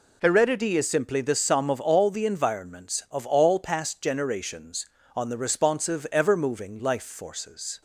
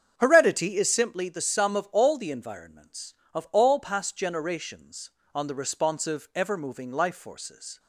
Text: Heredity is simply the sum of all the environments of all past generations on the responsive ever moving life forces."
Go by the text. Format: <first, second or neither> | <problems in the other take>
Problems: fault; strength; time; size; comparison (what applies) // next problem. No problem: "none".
first | starts louder than the rest; strong; until 1.1 s; 7.5 dB